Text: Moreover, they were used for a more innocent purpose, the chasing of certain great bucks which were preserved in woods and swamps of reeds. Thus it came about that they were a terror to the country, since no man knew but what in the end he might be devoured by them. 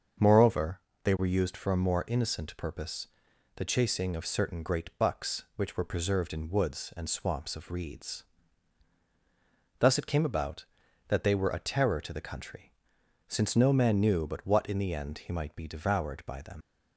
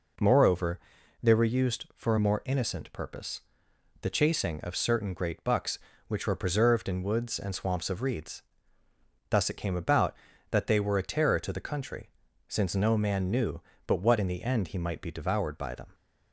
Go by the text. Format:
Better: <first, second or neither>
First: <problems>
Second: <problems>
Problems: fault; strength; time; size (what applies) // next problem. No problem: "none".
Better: second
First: starts louder than the rest; until 1.4 s; 6.5 dB // leaves "them" unfinished; at 16.6 s; 90 ms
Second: none